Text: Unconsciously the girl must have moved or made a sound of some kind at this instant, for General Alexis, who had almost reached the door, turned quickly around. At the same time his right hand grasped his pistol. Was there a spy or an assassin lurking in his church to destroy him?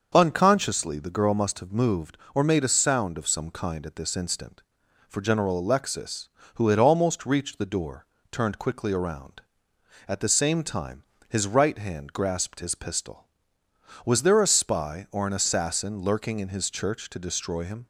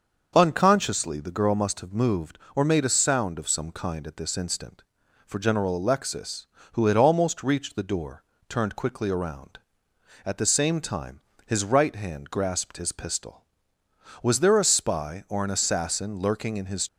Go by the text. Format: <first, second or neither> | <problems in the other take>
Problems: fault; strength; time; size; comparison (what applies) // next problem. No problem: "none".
first | starts louder than the rest; until 1.3 s; 6.5 dB; also in the first // pauses between "time" and "his"; slight; at 11.1 s; 0.26 s long; slight in the first // stops before "church to destroy him"; at 16.8 s